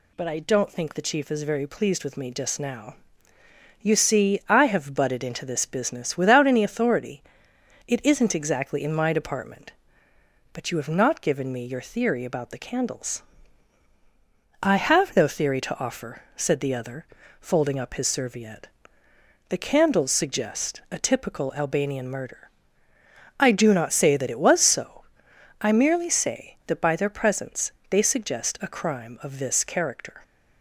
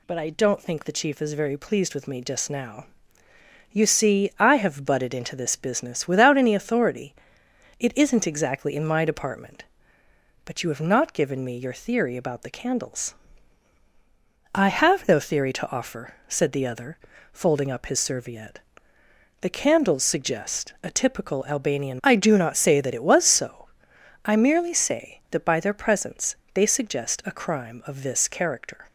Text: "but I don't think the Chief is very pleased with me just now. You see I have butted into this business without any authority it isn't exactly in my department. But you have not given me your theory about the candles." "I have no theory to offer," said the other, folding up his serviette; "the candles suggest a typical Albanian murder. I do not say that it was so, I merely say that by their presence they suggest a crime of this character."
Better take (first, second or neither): first